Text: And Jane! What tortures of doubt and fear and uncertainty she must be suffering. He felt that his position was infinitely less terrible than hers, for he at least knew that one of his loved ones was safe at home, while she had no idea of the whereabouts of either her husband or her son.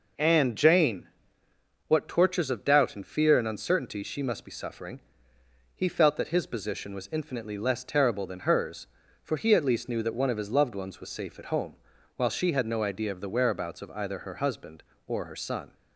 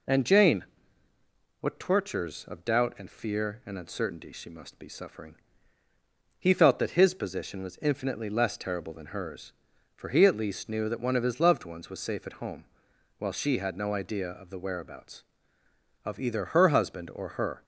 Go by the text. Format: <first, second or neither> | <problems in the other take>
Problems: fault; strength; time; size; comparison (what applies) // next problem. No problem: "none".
first | stops before "son"; at 17.6 s